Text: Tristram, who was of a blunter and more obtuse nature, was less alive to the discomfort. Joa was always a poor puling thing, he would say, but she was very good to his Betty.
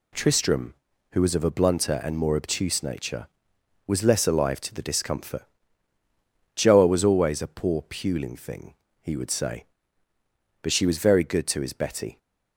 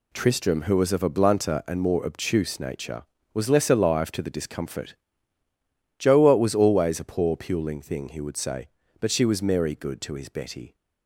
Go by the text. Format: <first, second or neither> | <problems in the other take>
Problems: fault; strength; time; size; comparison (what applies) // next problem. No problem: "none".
first | says "merry" for "very"; at 9.4 s